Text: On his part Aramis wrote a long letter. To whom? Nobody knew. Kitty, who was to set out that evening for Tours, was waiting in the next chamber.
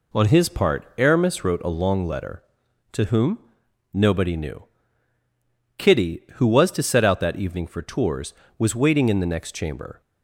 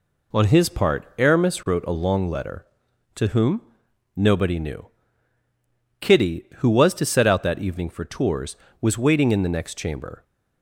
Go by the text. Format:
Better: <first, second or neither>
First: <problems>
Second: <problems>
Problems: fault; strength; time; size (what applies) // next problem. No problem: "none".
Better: neither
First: none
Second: none